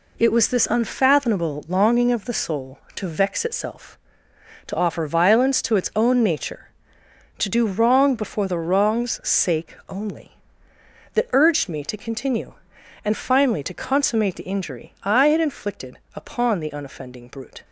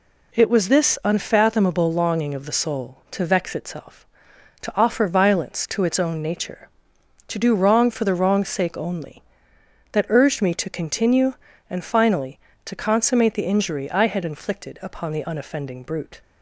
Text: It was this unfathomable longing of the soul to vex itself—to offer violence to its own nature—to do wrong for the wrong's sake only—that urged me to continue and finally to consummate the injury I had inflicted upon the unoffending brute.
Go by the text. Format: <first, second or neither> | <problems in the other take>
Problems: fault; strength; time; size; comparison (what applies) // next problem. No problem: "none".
second | says "before" for "for"; at 8.1 s // pauses between "inflicted" and "upon"; slight; at 15.9 s; 0.16 s long